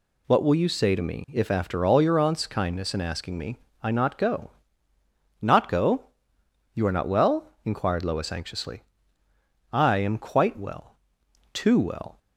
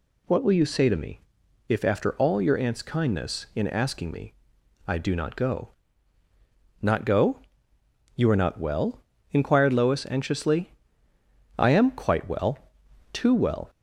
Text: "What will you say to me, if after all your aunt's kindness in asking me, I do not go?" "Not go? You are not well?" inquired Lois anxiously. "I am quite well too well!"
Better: second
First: skips "do"; at 3.9 s // pauses between "well" and "too"; noticeable; at 10.9 s; 0.58 s long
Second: pauses between "well" and "too"; noticeable; at 12.5 s; 0.56 s long

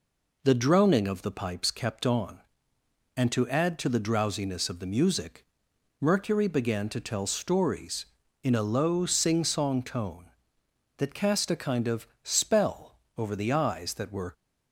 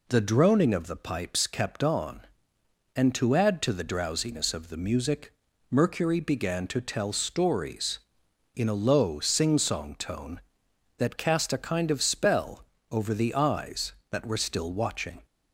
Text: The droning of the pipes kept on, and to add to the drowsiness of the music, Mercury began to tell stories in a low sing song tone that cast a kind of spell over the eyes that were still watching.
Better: second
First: pauses between "of" and "spell"; slight; at 12.0 s; 0.16 s long // pauses between "spell" and "over"; slight; at 12.9 s; 0.22 s long // stops before "still watching"; at 14.3 s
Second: pauses between "spell" and "over"; slight; at 12.6 s; 0.28 s long

